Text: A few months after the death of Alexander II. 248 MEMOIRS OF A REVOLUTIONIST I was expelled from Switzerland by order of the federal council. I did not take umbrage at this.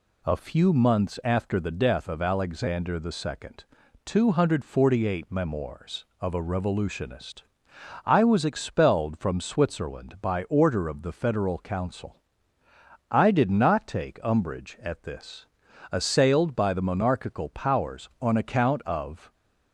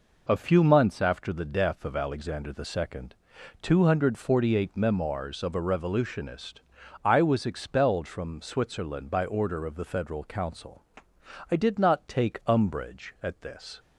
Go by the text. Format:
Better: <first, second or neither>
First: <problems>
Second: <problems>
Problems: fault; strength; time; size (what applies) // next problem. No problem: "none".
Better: second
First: pauses between "REVOLUTIONIST" and "I"; noticeable; at 7.4 s; 0.62 s long // goes on to say "Assailed by the monarchical powers on account of"; strong; from 15.9 s on; 3.4 s long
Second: pauses between "REVOLUTIONIST" and "I"; noticeable; at 6.5 s; 0.46 s long